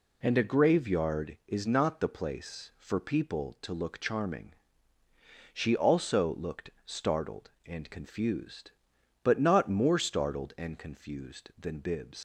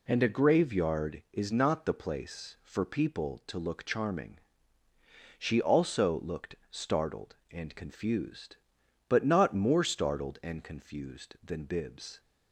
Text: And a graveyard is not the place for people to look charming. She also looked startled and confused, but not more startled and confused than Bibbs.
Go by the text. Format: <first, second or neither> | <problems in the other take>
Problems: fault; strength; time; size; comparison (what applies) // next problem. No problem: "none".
second | leaves "Bibbs" unfinished; at 12.1 s; 115 ms